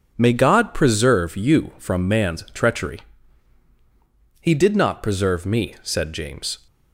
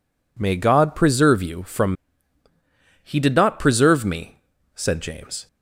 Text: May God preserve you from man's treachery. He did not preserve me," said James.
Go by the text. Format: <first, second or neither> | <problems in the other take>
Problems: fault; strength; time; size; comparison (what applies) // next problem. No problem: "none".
first | skips "man's treachery"; at 2.4 s